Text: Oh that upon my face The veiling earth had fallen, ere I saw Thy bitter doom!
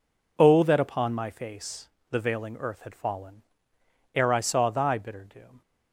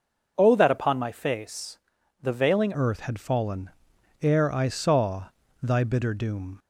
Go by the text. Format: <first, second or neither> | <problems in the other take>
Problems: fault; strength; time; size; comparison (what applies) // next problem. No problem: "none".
first | pauses between "face" and "The"; at 1.7 s; 0.44 s long; slight in the first // changes voice at "earth"; from 2.7 s on; 3.8 s long // pauses between "saw" and "Thy"; slight; at 5.2 s; 0.36 s long